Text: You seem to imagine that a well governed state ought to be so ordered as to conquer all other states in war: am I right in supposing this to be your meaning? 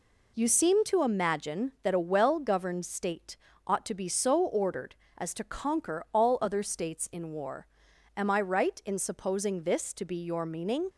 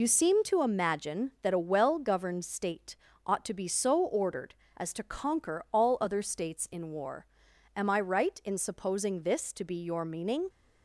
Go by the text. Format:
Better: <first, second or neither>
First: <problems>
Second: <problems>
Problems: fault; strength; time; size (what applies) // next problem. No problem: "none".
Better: first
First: pauses between "state" and "ought"; slight; at 3.3 s; 0.32 s long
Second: loses the start of "You"; at 0.0 s; 55 ms // pauses between "state" and "ought"; slight; at 2.9 s; 0.32 s long